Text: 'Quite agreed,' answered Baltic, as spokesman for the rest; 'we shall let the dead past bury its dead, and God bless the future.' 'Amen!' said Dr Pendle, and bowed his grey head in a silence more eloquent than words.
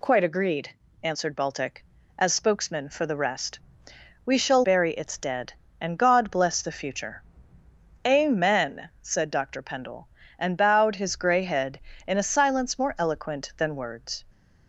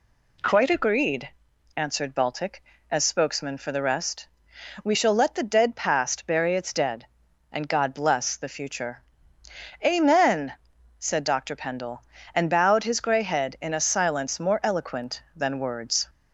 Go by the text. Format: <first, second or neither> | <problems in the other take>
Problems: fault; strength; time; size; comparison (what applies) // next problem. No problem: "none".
second | skips "let the dead past"; at 4.6 s